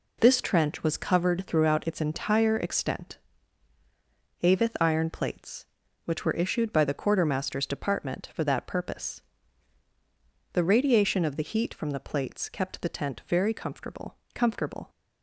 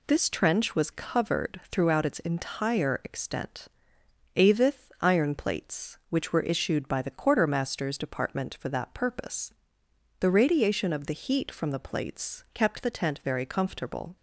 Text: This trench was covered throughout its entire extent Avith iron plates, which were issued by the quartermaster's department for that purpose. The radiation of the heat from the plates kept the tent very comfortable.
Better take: second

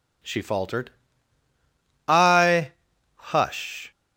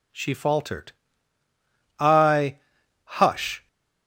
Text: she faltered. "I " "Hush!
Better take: neither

